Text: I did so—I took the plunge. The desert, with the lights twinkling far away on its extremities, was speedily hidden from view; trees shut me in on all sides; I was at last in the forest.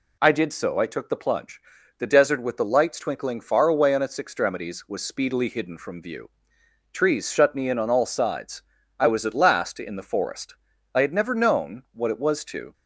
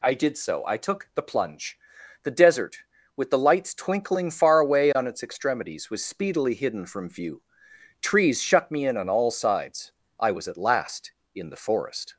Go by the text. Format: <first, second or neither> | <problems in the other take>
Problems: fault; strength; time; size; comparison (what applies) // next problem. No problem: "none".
second | goes on to say "I had never known what it was to"; strong; from 10.9 s on; 1.7 s long